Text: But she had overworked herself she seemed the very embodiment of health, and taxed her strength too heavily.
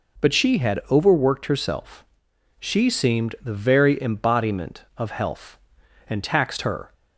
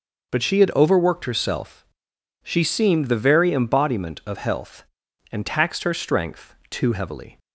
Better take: second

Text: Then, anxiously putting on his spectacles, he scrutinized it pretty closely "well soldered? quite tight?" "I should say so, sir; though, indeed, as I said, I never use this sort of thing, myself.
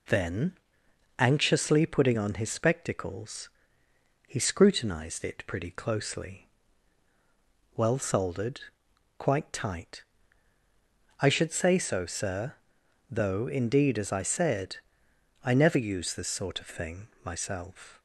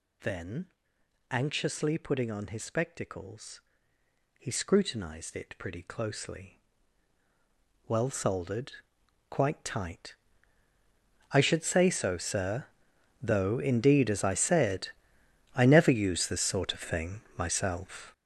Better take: first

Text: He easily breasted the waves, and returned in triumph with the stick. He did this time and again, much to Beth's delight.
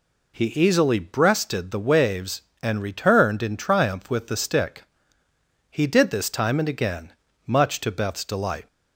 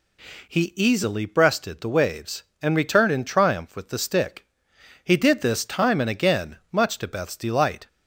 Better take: neither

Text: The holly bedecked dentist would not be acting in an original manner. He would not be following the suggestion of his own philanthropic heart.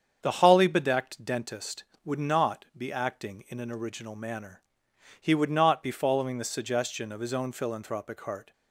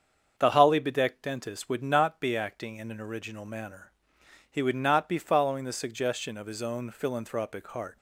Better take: neither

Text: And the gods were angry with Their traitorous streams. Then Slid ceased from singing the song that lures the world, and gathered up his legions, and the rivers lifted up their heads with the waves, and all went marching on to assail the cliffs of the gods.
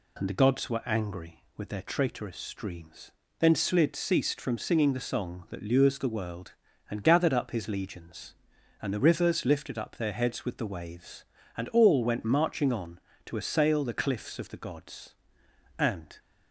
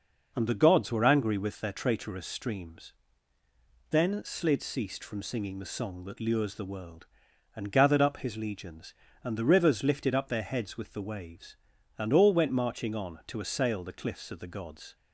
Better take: second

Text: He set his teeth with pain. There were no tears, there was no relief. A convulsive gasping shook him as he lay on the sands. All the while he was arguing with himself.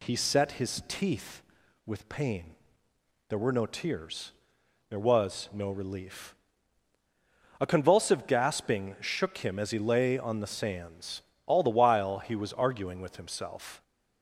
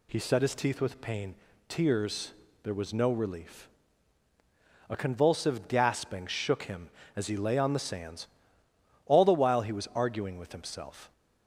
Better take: first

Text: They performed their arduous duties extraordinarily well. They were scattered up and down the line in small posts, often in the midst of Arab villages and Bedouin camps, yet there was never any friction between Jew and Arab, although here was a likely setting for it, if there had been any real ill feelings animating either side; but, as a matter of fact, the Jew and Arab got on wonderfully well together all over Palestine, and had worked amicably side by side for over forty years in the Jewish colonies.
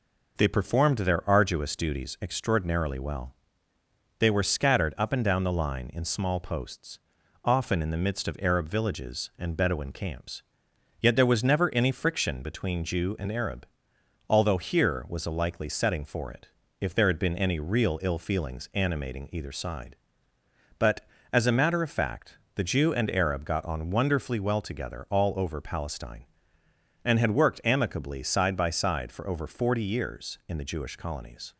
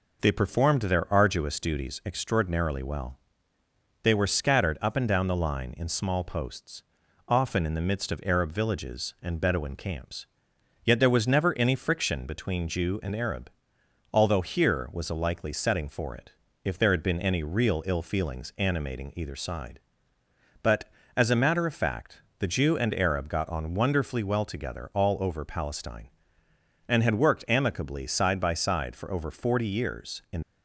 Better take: first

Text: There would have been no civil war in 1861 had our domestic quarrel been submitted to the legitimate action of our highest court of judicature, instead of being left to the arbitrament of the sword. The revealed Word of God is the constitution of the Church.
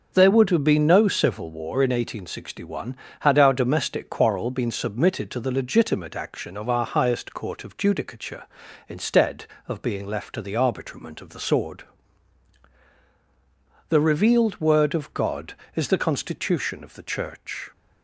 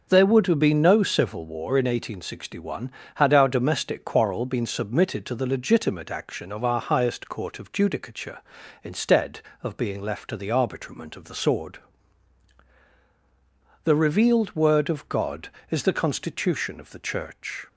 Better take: neither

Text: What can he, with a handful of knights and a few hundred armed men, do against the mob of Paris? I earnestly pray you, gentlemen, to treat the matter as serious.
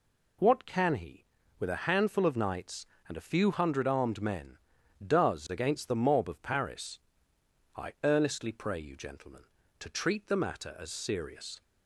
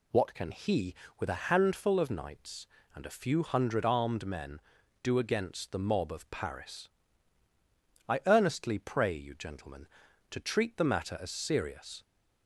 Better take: second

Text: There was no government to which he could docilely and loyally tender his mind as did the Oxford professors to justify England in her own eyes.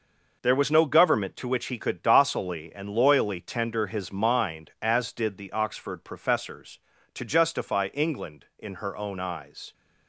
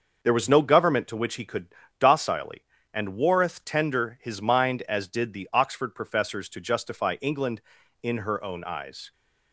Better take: first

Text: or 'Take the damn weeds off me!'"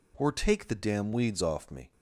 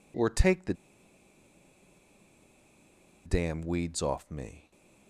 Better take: first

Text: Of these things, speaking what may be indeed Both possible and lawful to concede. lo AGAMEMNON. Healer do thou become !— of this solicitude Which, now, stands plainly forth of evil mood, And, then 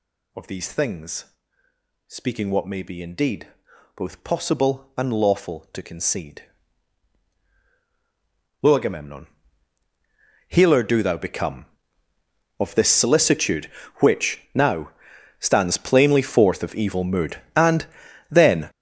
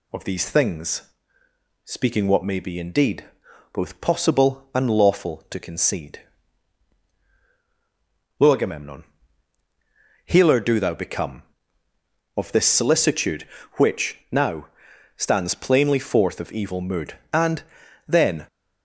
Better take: second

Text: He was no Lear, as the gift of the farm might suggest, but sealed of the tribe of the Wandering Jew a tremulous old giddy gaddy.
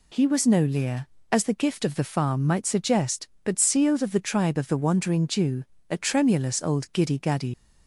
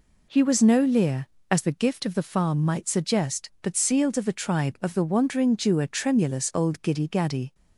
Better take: second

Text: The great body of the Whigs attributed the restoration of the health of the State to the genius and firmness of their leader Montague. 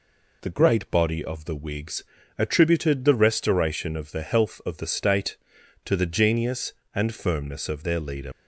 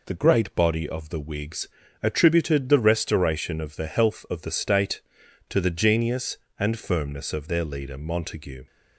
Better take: second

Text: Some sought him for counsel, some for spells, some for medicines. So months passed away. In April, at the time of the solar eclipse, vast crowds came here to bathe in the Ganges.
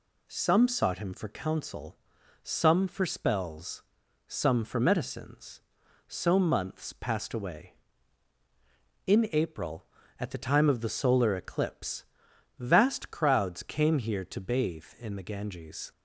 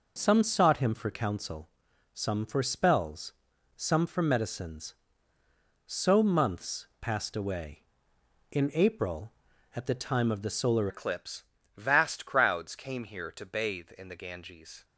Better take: first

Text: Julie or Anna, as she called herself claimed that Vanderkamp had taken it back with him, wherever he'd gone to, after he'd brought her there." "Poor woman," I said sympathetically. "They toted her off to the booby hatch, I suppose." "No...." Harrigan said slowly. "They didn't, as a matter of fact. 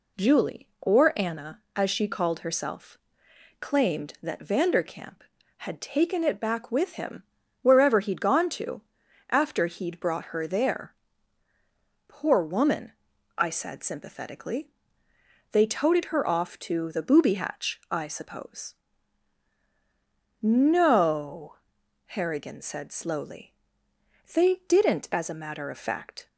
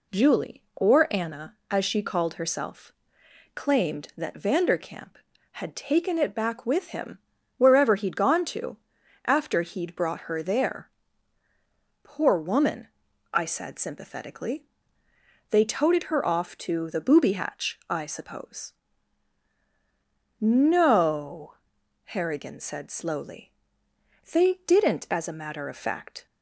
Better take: neither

